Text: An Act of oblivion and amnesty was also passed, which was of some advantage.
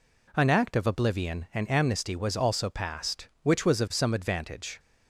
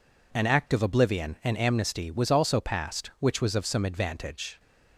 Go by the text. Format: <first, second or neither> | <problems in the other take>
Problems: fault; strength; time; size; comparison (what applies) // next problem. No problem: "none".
neither | none